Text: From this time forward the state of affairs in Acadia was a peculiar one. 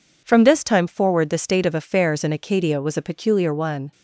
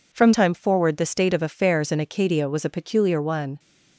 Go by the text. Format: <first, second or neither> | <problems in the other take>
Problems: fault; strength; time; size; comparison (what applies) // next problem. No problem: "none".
first | skips "this"; at 0.3 s